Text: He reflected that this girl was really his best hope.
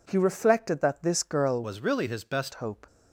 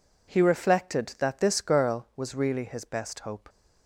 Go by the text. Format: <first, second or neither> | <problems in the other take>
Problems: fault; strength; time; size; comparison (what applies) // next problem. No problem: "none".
second | changes voice from "was" to "best"; from 1.6 to 2.5 s; 0.9 s long